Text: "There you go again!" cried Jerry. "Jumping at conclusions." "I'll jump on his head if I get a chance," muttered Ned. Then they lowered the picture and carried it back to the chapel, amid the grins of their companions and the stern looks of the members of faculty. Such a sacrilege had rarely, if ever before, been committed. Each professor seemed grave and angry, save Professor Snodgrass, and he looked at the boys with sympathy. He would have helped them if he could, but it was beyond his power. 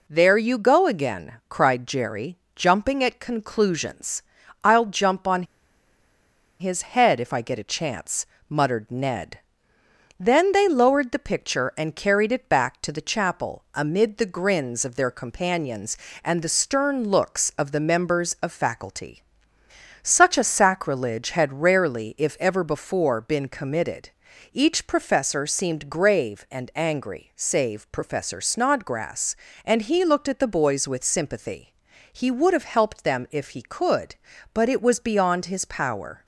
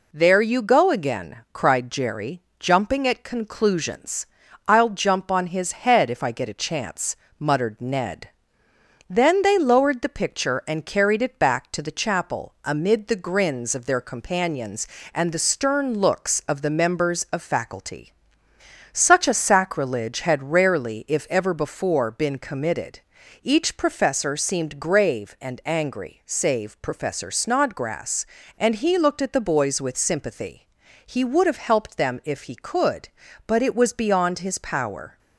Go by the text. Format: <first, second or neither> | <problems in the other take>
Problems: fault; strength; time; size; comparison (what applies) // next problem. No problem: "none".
second | pauses between "on" and "his"; at 5.4 s; 1.1 s long